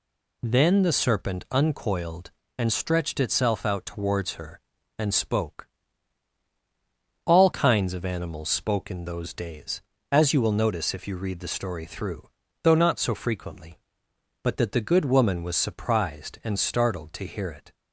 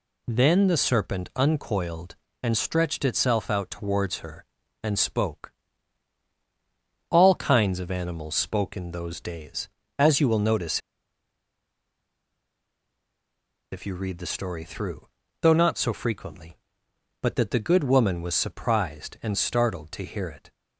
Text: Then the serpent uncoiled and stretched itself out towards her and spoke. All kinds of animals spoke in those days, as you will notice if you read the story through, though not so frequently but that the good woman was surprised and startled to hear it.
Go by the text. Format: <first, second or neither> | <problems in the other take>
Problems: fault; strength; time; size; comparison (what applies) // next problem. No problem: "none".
first | pauses between "notice" and "if"; strong; at 10.8 s; 2.9 s long